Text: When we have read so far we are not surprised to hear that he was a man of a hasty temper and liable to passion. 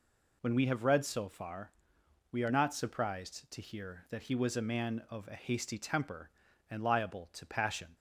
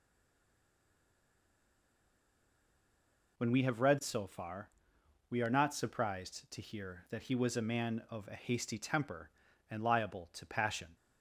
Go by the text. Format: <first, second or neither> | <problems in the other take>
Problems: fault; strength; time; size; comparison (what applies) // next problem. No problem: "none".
first | stays silent before the first word; strong; until 3.3 s; 3.3 s long // pauses between "far" and "we"; noticeable; at 4.6 s; 0.60 s long; noticeable in the first